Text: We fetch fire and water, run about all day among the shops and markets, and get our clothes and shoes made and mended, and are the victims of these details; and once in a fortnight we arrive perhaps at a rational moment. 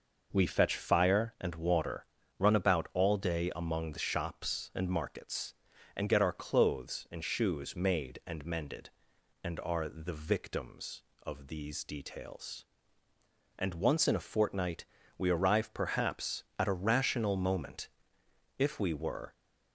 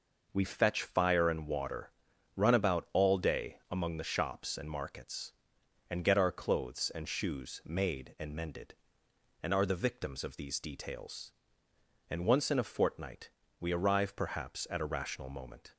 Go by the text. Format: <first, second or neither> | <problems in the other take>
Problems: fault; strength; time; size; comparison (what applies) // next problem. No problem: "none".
second | pauses between "fortnight" and "we"; slight; at 14.8 s; 0.32 s long; slight in the second // goes on to say "If we were"; noticeable; from 18.5 s on; 0.76 s long